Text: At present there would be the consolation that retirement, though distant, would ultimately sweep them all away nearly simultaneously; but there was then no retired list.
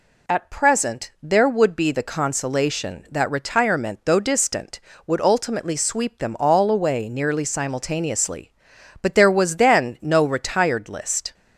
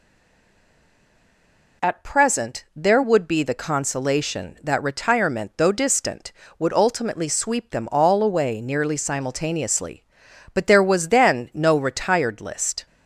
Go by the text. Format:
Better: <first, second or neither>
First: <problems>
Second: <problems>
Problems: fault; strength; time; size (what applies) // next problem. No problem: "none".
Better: first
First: none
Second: stays silent before the first word; noticeable; until 1.8 s; 1.8 s long